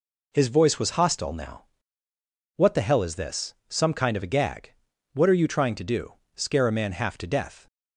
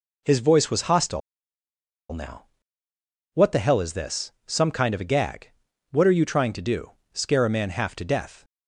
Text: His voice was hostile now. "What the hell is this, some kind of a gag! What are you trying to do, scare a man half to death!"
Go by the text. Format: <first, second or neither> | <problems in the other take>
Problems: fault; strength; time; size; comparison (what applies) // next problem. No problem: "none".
first | pauses between "hostile" and "now"; noticeable; at 1.2 s; 0.91 s long